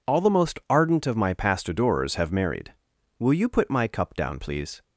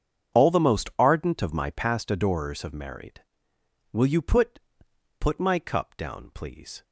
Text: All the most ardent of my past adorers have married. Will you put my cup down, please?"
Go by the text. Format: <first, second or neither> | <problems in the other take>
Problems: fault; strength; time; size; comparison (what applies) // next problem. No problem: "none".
first | starts louder than the rest; strong; until 1.4 s; 7.5 dB // says "put" twice; at 5.1 s